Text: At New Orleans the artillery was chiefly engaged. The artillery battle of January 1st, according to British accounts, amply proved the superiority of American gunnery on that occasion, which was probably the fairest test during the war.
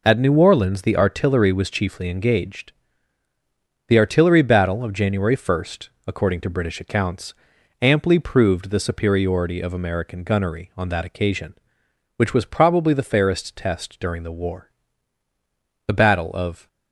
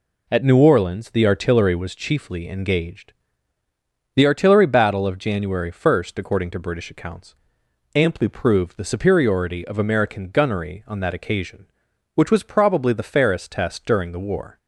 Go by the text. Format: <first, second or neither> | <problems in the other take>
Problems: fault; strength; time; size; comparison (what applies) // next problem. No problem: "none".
second | goes on to say "The battle of"; noticeable; from 15.8 s on; 0.80 s long